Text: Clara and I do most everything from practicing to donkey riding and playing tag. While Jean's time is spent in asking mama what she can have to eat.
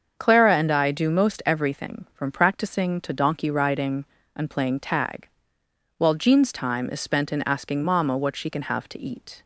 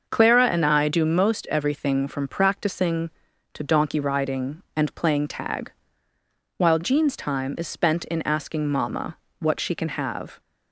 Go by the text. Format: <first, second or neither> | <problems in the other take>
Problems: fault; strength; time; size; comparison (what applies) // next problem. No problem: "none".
first | starts louder than the rest; until 1.1 s; 6.5 dB; also in the first // pauses between "mama" and "what"; slight; at 9.1 s; 0.22 s long // stops before "to eat"; at 10.3 s